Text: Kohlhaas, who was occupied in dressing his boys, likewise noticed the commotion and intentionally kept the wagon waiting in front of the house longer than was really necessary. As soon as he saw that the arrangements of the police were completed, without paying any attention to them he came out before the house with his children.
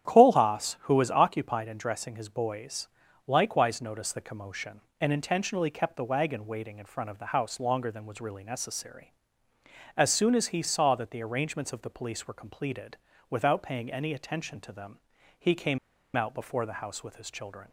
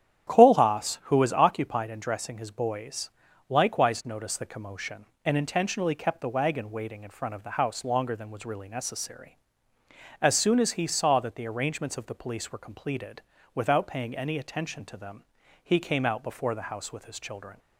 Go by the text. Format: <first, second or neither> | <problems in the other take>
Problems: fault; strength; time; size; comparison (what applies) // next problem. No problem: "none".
second | starts louder than the rest; strong; until 1.1 s; 10 dB; strong in the second // pauses between "them" and "he"; at 15.0 s; 0.38 s long; also in the second // pauses between "came" and "out"; at 15.7 s; 0.37 s long